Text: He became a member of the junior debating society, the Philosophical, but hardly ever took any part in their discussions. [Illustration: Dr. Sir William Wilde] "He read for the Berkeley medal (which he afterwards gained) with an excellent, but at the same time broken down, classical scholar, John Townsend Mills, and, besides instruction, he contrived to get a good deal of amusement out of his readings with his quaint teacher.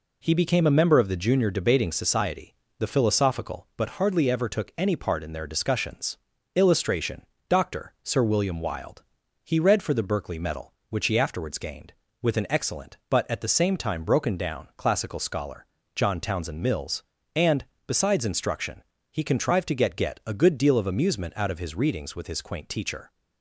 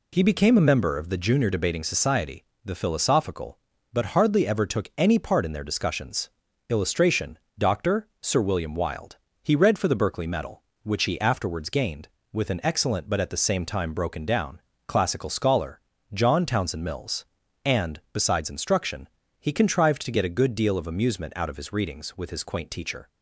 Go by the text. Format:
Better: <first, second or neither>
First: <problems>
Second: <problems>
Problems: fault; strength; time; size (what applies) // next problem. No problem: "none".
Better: second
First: pauses between "Wilde" and "He"; at 9.0 s; 0.42 s long // says "get" twice; at 19.9 s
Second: pauses between "Wilde" and "He"; slight; at 9.1 s; 0.26 s long